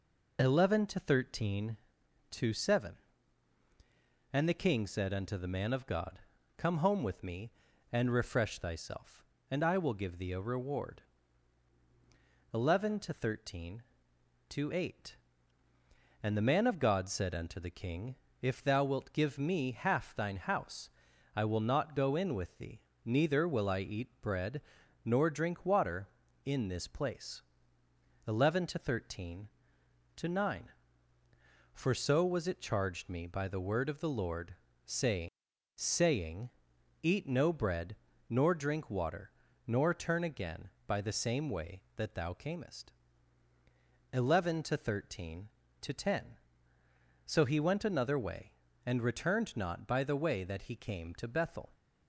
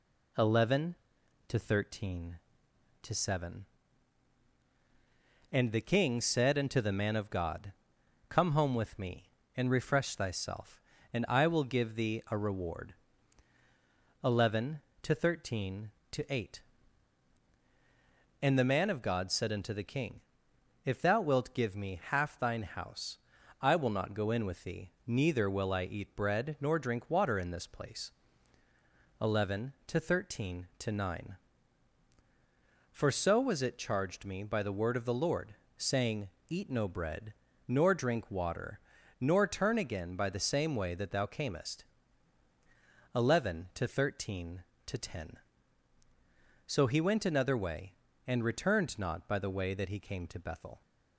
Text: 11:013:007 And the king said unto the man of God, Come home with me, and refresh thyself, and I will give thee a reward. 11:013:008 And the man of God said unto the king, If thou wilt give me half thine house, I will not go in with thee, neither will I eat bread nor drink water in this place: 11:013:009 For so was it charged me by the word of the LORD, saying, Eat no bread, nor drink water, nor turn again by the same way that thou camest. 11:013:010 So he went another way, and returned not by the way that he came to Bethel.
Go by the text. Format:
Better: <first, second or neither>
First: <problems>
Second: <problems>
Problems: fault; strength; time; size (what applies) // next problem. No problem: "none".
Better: second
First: pauses between "bread" and "nor"; at 24.6 s; 0.42 s long // says "saying" twice; at 35.7 s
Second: none